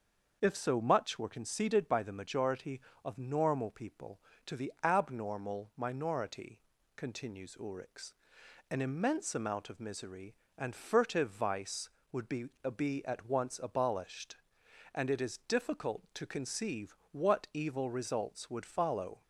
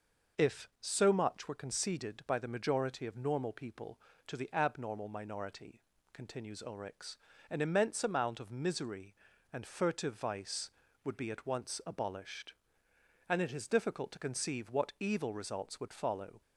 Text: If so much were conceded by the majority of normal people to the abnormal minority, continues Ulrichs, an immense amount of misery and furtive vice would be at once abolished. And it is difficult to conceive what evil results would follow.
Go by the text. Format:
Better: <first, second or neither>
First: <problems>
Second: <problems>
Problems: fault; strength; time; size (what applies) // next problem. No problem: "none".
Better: second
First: starts louder than the rest; until 1.4 s; 6 dB // says "be" twice; at 12.7 s // pauses between "conceive" and "what"; slight; at 16.9 s; 0.16 s long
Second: none